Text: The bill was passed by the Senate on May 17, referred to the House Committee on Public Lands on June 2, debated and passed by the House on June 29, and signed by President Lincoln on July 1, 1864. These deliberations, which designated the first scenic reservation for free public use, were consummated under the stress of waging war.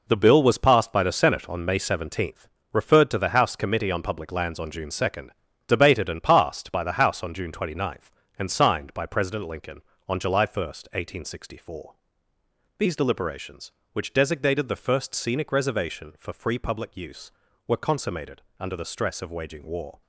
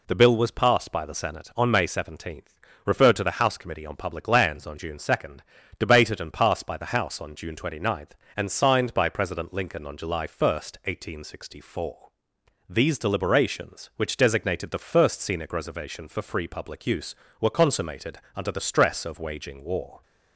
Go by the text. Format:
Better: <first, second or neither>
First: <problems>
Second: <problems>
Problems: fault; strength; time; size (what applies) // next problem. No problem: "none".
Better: second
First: gets quieter; strong; throughout; 9 dB // pauses between "consummated" and "under"; slight; at 18.4 s; 0.16 s long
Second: pauses between "consummated" and "under"; slight; at 18.1 s; 0.18 s long